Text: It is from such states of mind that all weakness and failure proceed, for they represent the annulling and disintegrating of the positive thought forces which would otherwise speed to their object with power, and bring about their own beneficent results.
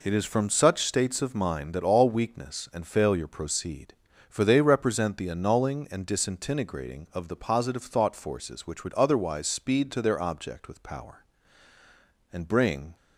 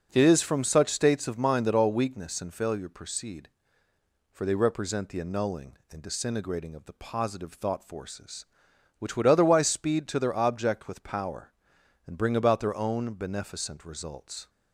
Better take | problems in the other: second | stops before "about their own beneficent results"; at 12.9 s

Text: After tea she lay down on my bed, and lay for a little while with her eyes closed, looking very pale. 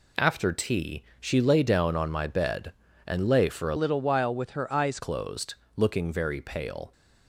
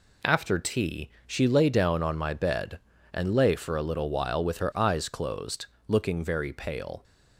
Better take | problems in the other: second | pauses between "tea" and "she"; slight; at 1.0 s; 0.16 s long; slight in the second // changes voice from "little" to "eyes"; from 3.7 to 4.9 s; 1.2 s long

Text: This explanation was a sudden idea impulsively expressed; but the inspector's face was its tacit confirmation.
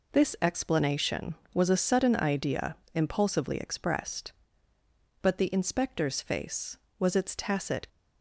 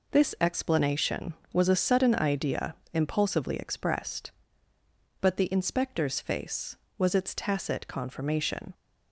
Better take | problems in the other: second | pauses between "idea" and "impulsively"; slight; at 2.7 s; 0.18 s long; slight in the second // stops before "confirmation"; at 7.8 s

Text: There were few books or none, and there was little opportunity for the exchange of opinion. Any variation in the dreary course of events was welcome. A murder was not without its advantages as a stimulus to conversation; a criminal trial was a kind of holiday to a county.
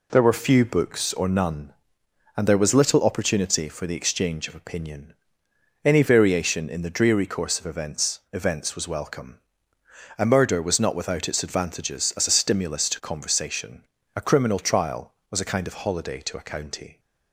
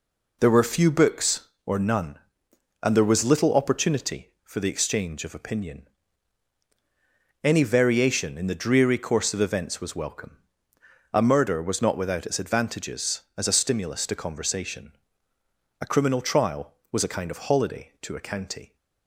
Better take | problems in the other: second | says "events" twice; at 8.3 s

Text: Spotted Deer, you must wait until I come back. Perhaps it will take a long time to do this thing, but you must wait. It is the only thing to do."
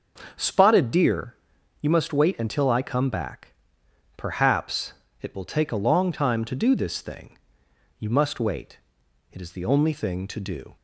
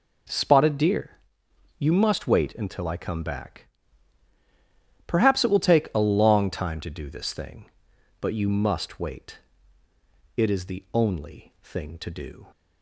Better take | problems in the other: second | starts louder than the rest; until 1.8 s; 6.5 dB // pauses between "Perhaps" and "it"; slight; at 4.9 s; 0.28 s long // skips "but"; at 7.6 s

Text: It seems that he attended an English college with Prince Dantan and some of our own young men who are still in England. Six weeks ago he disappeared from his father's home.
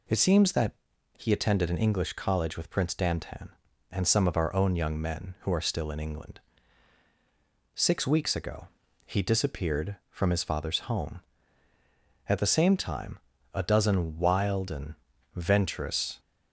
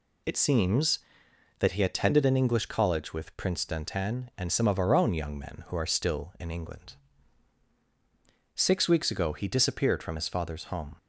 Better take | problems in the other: second | pauses between "that" and "he"; at 0.7 s; 0.44 s long // pauses between "ago" and "he"; at 8.6 s; 0.38 s long // goes on to say "At the same time a dozen wild and venturous"; strong; from 12.2 s on; 3.9 s long

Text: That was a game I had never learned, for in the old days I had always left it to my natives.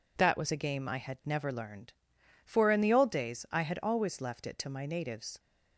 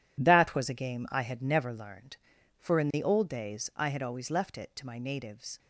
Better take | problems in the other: first | gets quieter; strong; throughout; 9.5 dB

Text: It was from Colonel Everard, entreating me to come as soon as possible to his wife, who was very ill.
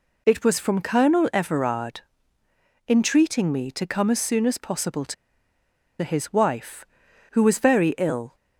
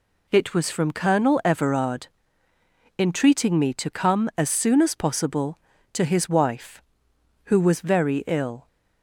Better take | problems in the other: second | pauses between "to" and "his"; noticeable; at 5.1 s; 0.87 s long

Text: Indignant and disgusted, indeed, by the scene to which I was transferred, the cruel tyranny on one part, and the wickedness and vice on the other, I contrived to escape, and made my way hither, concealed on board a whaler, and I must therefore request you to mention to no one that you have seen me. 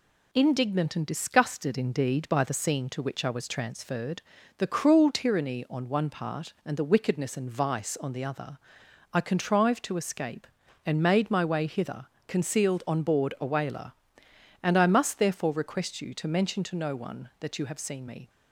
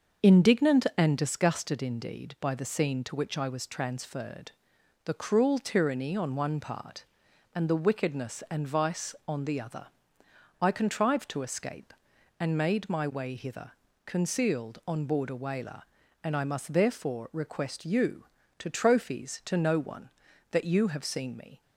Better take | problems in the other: first | starts louder than the rest; until 1.3 s; 6.5 dB // says "trophies" for "mention"; at 18.6 s

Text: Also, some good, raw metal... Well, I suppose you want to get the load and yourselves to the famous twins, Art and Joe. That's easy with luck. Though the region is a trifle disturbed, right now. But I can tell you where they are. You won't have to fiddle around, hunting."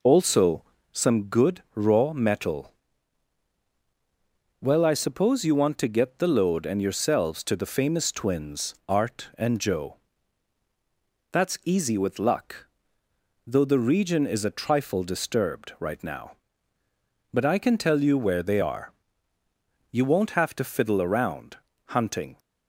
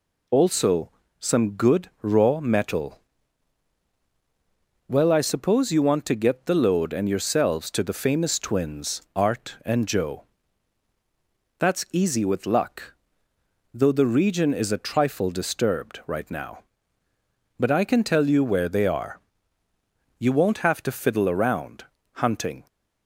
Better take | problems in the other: second | starts louder than the rest; noticeable; until 1.2 s; 4.5 dB

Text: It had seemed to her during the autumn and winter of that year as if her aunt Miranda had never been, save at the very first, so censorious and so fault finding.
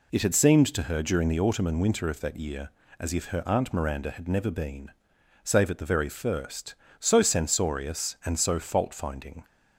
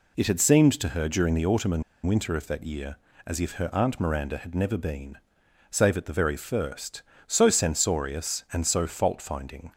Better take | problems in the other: first | pauses between "and" and "winter"; slight; at 1.8 s; 0.23 s long

